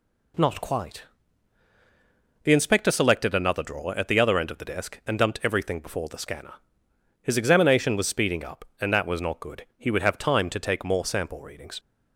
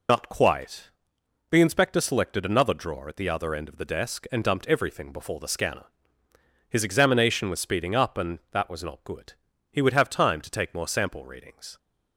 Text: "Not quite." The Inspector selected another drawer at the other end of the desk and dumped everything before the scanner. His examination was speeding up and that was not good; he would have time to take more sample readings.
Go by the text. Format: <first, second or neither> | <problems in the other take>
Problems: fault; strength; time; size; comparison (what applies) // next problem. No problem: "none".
first | loses the start of "Not"; at 0.0 s; 95 ms